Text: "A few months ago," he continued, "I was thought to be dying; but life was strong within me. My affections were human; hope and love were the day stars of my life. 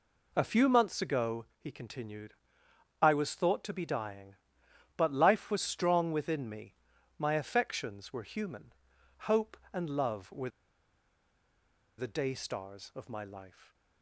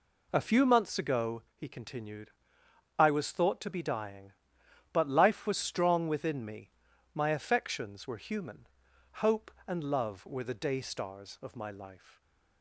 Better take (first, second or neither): second